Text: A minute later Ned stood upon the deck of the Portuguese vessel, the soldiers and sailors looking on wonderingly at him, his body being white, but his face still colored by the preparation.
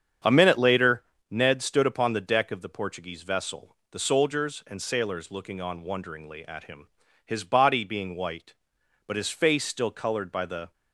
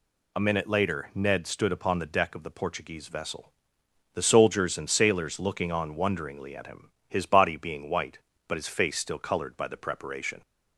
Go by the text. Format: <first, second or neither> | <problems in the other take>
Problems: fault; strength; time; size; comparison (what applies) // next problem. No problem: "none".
second | starts louder than the rest; strong; until 1.5 s; 8 dB // pauses between "later" and "Ned"; slight; at 1.0 s; 0.26 s long // stops before "preparation"; at 10.7 s